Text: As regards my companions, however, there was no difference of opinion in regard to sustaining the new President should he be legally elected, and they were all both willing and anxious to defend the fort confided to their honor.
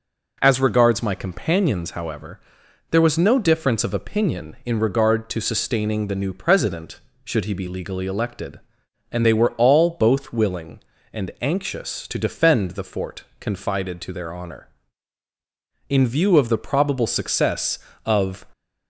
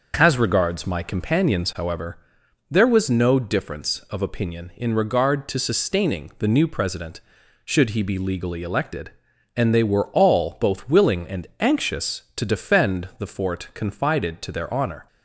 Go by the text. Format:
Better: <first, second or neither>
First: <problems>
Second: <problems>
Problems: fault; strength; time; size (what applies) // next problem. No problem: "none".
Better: second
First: pauses between "fort" and "confided"; slight; at 13.2 s; 0.16 s long // goes on to say "In view of the probable success of"; strong; from 15.8 s on; 2.5 s long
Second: none